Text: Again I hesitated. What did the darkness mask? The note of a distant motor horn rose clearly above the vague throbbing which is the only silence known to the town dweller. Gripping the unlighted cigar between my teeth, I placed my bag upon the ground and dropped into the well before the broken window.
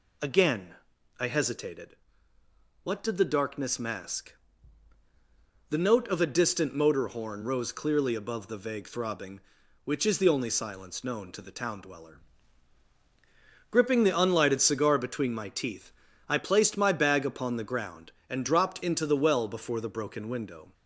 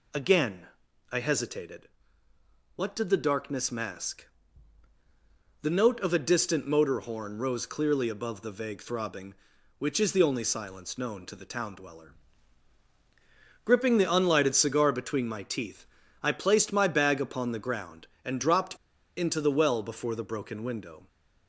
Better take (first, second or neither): first